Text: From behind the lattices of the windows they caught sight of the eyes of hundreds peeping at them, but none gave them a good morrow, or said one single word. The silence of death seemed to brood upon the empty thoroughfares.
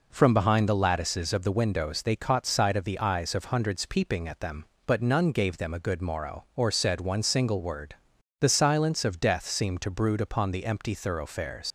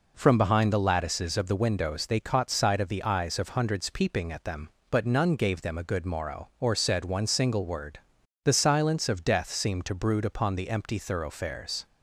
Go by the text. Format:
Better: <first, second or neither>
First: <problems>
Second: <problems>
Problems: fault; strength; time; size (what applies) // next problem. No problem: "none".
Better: second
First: leaves "thoroughfares" unfinished; at 11.6 s; 110 ms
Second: none